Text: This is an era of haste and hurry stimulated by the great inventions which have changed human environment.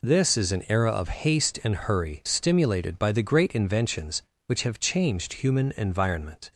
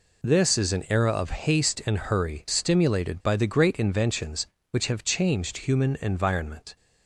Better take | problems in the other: neither | none

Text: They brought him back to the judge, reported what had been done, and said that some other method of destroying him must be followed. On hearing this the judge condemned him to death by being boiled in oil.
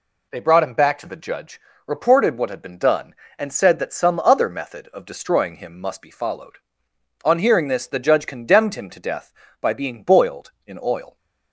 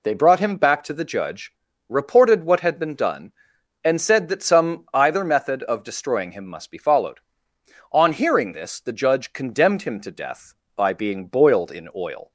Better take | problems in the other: first | says "either" for "other"; at 4.9 s

